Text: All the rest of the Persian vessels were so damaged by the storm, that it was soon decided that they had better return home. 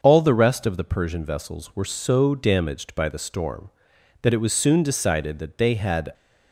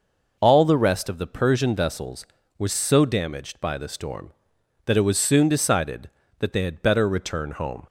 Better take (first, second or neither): second